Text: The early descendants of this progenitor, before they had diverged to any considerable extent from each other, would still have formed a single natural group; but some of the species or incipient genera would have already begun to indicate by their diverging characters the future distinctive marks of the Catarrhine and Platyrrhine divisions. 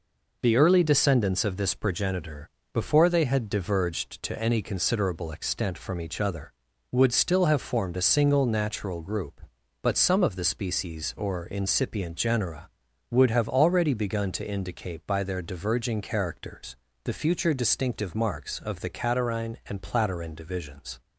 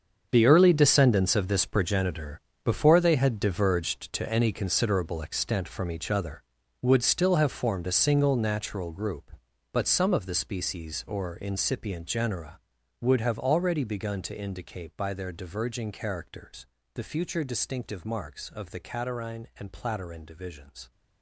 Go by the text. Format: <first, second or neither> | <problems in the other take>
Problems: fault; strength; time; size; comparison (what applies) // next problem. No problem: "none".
first | gets quieter; strong; throughout; 13.5 dB // pauses between "characters" and "the"; slight; at 16.6 s; 0.26 s long; slight in the first